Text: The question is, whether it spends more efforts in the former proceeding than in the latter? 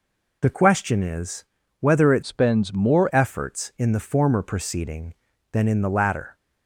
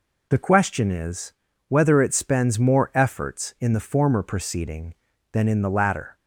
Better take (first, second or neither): second